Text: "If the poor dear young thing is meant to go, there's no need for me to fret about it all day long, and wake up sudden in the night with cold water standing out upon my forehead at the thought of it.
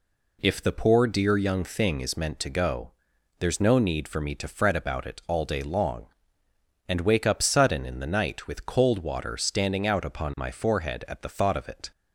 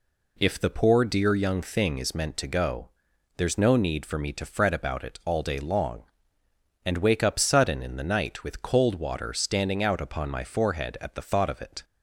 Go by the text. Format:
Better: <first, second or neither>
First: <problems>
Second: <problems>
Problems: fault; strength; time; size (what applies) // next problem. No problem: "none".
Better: neither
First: none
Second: none